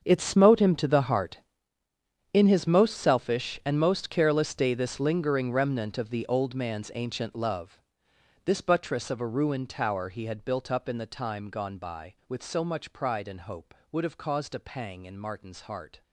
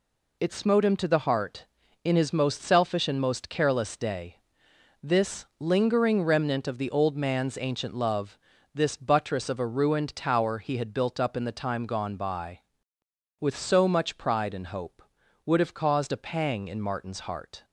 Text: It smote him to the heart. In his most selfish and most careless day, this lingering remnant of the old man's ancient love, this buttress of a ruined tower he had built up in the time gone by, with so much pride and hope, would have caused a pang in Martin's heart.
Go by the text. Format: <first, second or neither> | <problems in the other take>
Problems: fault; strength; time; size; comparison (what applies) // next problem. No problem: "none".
second | gets quieter; strong; throughout; 17 dB